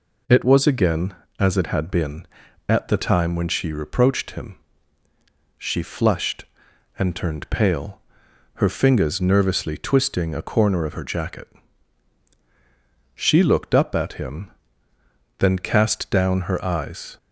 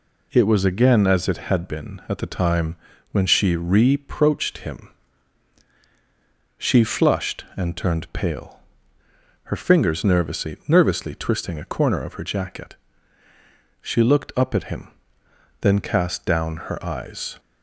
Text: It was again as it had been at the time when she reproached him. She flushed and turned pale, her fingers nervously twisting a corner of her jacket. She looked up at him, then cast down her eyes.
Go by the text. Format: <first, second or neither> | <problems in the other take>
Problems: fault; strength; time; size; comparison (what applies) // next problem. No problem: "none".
first | pauses between "time" and "when"; slight; at 2.7 s; 0.36 s long // says "nervously" twice; at 10.6 s